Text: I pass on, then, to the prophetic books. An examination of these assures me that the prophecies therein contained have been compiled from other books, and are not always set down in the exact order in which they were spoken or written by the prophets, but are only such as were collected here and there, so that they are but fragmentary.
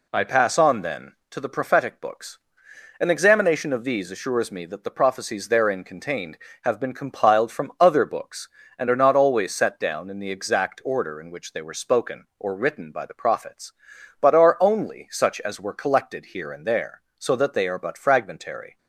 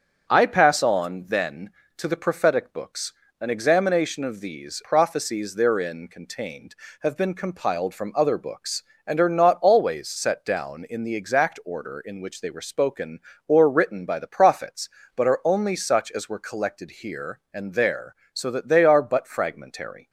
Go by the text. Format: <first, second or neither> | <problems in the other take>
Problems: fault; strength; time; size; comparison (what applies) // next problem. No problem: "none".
first | starts louder than the rest; until 1.3 s; 7 dB // skips "assures me that the"; at 4.8 s